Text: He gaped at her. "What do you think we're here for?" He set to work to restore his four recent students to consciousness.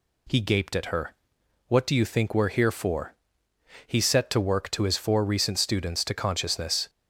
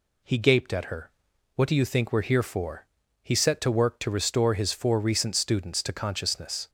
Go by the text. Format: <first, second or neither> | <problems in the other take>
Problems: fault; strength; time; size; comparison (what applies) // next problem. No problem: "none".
second | skips "restore"; at 4.8 s